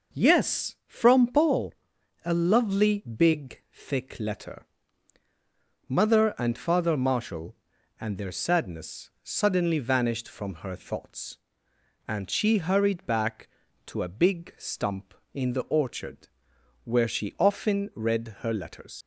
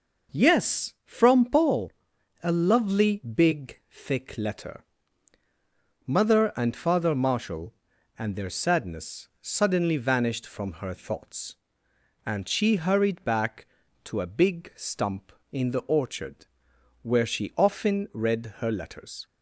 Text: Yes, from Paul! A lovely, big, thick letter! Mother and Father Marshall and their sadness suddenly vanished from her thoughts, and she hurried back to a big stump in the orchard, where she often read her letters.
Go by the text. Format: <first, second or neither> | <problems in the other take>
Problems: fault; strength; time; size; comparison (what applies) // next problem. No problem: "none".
second | leaves "letters" unfinished; at 19.0 s; 60 ms